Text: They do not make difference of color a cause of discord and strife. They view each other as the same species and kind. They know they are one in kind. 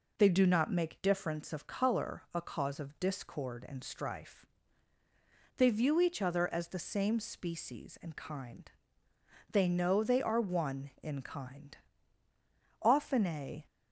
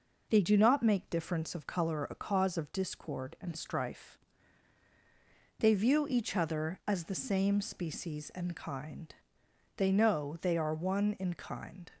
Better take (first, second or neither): second